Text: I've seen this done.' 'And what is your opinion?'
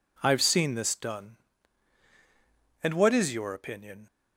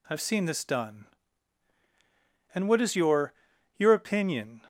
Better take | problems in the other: first | says "your" twice; at 3.7 s

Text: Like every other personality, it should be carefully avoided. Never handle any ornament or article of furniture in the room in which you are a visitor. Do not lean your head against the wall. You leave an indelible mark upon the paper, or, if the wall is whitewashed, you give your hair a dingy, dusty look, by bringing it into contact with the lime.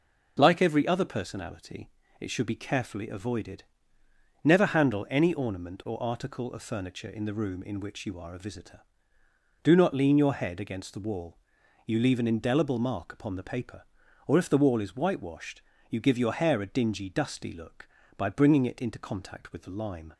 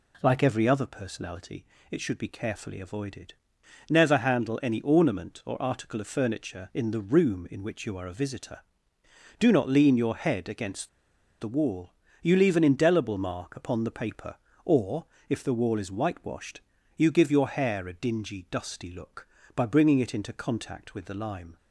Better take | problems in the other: first | pauses between "against" and "the"; noticeable; at 10.8 s; 0.51 s long

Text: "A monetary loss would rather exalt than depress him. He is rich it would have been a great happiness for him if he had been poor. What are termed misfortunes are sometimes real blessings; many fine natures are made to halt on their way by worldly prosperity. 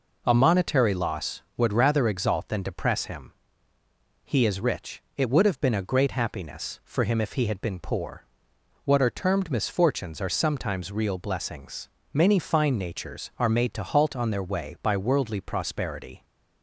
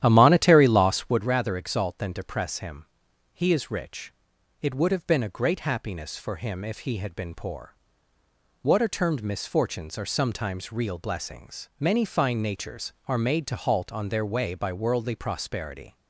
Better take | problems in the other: first | starts louder than the rest; strong; until 1.3 s; 11.5 dB // pauses between "rich" and "it"; noticeable; at 4.1 s; 0.46 s long; slight in the first

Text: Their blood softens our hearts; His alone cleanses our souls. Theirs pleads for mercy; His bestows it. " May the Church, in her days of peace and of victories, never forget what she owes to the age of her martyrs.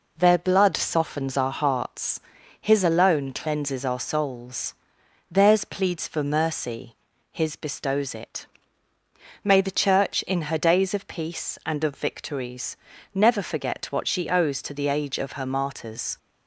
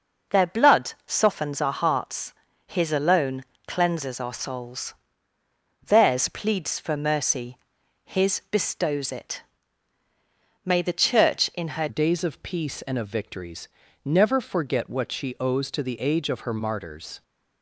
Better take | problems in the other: first | starts louder than the rest; until 1.4 s; 7 dB // pauses between "alone" and "cleanses"; slight; at 3.4 s; 0.22 s long // changes voice at "days"; from 11.8 s on; 5.4 s long

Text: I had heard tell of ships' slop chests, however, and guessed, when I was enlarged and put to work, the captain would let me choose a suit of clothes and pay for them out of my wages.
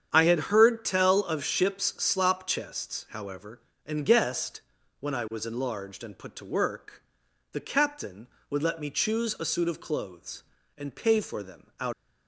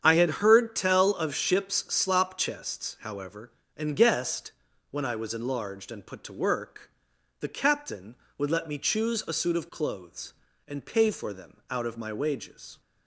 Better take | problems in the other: second | starts louder than the rest; strong; until 1.1 s; 8.5 dB; strong in the second // stops before "of my wages"; at 11.9 s

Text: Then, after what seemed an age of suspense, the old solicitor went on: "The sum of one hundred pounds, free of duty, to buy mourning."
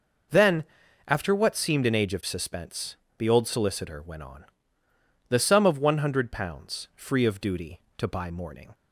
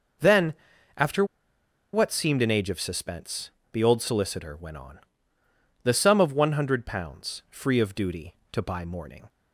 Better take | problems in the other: first | pauses between "after" and "what"; noticeable; at 1.2 s; 0.69 s long

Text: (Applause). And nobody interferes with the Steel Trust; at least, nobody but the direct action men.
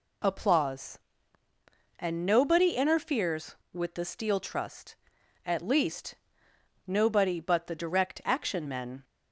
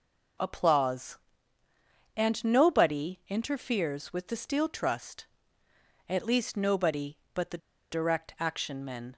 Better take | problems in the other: first | pauses between "the" and "direct"; slight; at 7.5 s; 0.32 s long

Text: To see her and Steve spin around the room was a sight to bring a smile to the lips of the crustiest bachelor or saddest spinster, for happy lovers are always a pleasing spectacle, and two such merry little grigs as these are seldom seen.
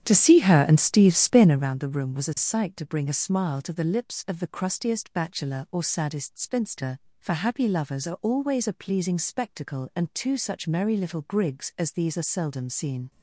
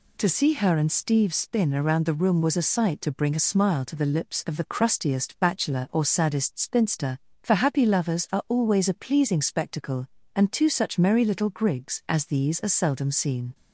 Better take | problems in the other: second | starts louder than the rest; strong; until 1.8 s; 9.5 dB

